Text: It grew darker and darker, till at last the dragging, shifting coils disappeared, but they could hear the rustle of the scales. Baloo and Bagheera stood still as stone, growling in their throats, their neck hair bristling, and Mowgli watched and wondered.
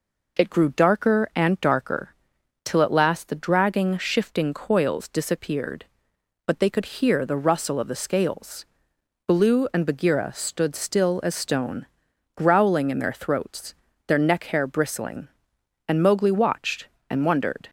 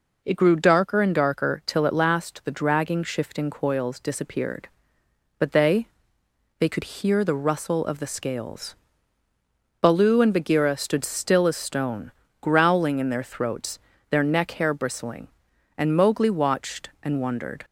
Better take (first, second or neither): first